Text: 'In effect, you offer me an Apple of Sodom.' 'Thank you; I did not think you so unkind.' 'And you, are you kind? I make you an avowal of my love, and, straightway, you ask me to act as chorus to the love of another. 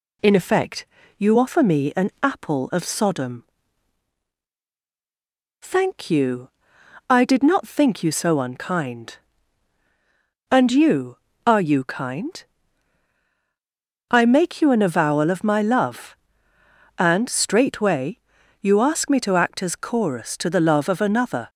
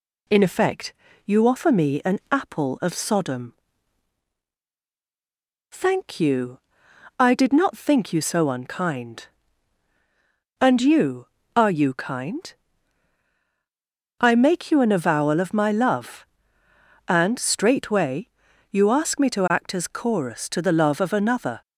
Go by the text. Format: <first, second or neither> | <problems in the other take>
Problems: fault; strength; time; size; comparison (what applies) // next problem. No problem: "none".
neither | none